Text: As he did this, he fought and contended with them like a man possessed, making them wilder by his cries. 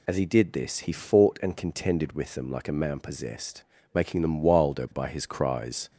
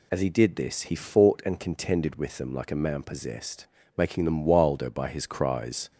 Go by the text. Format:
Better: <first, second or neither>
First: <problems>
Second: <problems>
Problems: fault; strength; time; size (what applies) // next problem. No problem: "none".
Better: neither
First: none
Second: none